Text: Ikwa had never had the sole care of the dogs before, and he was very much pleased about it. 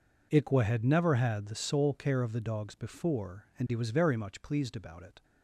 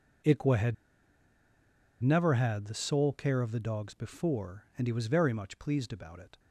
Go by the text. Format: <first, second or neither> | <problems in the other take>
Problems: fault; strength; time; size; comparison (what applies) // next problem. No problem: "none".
first | pauses between "had" and "never"; strong; at 0.7 s; 1.2 s long